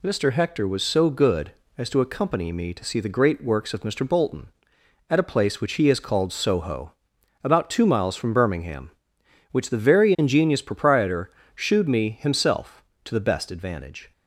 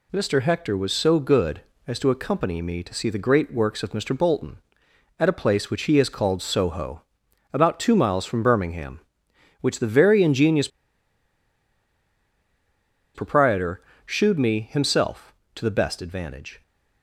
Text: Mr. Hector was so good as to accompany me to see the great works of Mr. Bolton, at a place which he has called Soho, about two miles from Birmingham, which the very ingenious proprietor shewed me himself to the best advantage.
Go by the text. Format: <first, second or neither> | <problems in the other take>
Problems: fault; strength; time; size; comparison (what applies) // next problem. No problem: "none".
first | pauses between "ingenious" and "proprietor"; strong; at 10.6 s; 2.4 s long // pauses between "proprietor" and "shewed"; slight; at 13.8 s; 0.24 s long; slight in the first